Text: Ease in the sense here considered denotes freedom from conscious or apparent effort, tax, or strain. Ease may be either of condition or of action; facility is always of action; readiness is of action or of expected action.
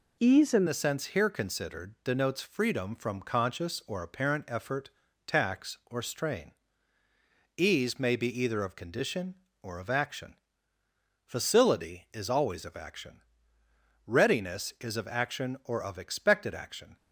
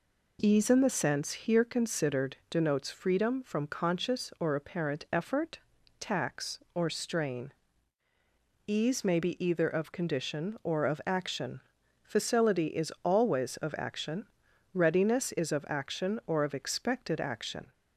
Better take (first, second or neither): second